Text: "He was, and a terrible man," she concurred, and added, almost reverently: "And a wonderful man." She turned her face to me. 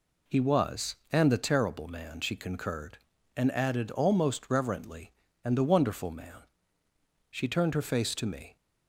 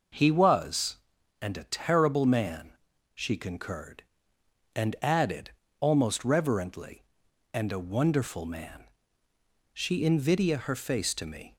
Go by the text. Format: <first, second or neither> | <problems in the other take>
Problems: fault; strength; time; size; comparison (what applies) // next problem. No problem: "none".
first | says "invidia" for "turned"; at 10.0 s